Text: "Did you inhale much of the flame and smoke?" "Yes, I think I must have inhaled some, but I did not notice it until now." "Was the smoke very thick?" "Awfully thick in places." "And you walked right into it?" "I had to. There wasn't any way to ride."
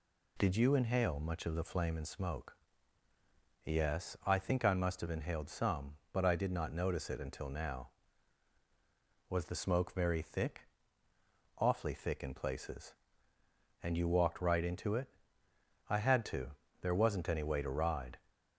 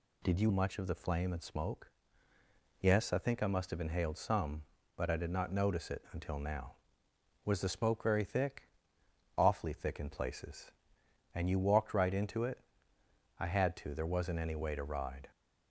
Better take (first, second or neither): first